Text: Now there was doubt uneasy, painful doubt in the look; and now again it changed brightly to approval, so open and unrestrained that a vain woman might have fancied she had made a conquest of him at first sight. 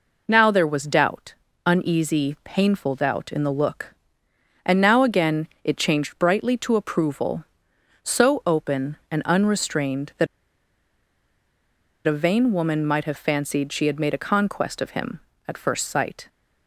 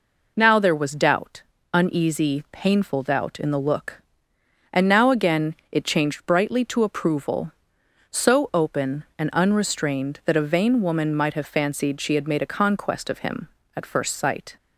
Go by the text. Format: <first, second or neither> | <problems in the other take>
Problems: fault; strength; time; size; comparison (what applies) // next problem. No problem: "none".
second | pauses between "doubt" and "uneasy"; slight; at 1.3 s; 0.32 s long; slight in the second // pauses between "again" and "it"; slight; at 5.4 s; 0.18 s long; slight in the second // pauses between "that" and "a"; strong; at 10.2 s; 1.8 s long